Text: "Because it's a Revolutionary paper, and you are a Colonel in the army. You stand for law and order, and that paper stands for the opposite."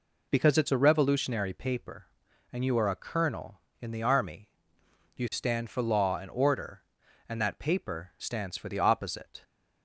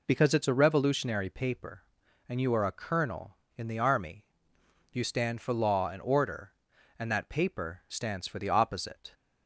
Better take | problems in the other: neither | none

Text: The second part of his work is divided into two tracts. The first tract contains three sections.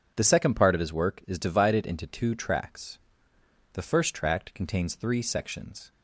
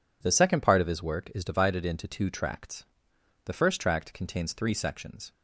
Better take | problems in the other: neither | none

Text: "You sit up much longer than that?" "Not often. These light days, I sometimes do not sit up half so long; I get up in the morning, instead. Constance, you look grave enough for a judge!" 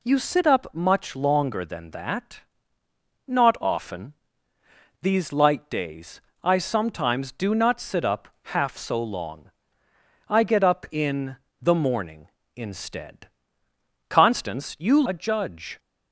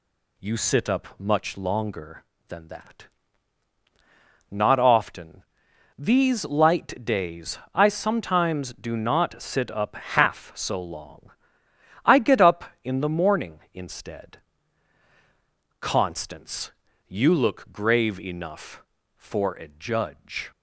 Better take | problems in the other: second | pauses between "up" and "half"; slight; at 8.2 s; 0.24 s long // pauses between "in" and "the"; slight; at 11.3 s; 0.24 s long // skips "look grave enough for"; at 15.0 s

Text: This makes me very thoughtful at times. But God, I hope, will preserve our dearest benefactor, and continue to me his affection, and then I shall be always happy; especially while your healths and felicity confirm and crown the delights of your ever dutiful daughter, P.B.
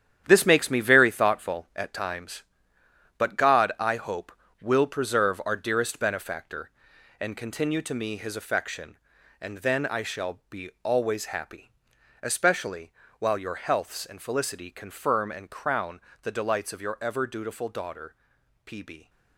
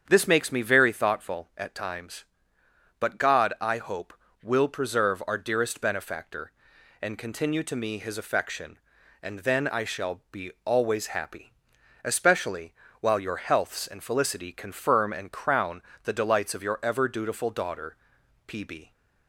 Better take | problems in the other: second | gets quieter; strong; throughout; 9 dB // starts louder than the rest; strong; until 1.2 s; 10 dB; strong in the second // pauses between "especially" and "while"; slight; at 12.9 s; 0.26 s long; slight in the second // pauses between "crown" and "the"; slight; at 15.9 s; 0.22 s long; slight in the second

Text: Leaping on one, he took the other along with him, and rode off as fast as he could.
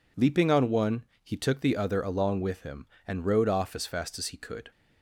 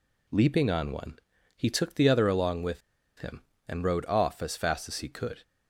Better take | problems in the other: first | pauses between "with" and "him"; at 2.8 s; 0.38 s long

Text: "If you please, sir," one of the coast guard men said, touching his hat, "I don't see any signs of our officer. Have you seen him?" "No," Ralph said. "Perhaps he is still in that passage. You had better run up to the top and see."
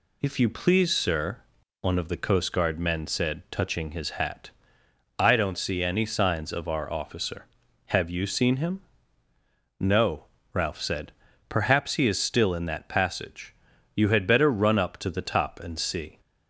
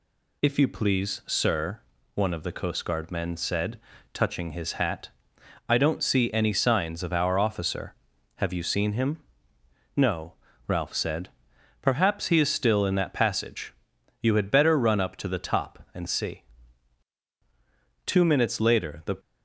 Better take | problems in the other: first | goes on to say "Two minutes later the"; noticeable; from 18.0 s on; 1.1 s long

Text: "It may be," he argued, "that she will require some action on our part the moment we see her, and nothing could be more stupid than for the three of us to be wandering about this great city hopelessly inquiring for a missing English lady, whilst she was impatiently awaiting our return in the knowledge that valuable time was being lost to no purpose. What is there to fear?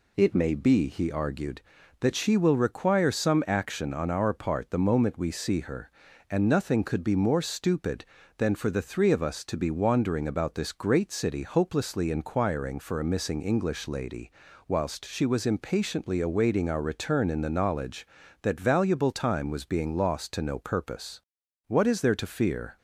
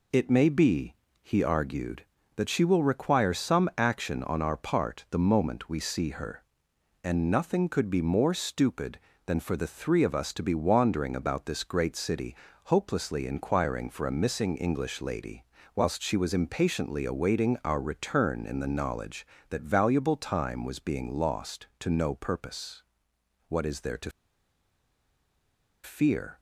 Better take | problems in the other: first | pauses between "city" and "hopelessly"; slight; at 12.3 s; 0.30 s long // pauses between "to" and "fear"; strong; at 24.1 s; 1.7 s long

